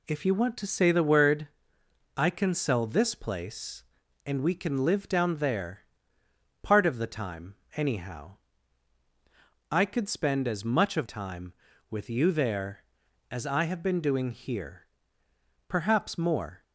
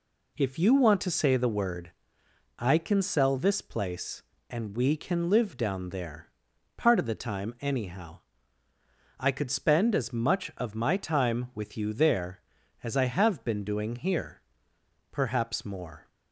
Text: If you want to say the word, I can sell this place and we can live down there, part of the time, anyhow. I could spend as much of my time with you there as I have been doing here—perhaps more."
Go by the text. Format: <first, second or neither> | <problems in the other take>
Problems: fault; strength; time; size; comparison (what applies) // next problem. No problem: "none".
second | skips "my"; at 11.0 s